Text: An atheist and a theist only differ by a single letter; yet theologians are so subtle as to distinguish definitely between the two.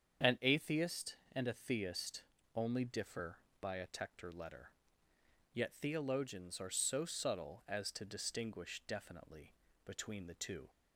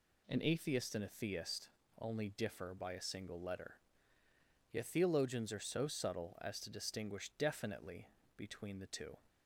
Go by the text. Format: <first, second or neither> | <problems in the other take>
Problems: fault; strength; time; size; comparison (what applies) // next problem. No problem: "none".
second | starts louder than the rest; strong; until 1.4 s; 7.5 dB // pauses between "theist" and "only"; slight; at 2.2 s; 0.32 s long; slight in the second // says "tector" for "single"; at 3.8 s // pauses between "definitely" and "between"; slight; at 9.5 s; 0.32 s long; slight in the second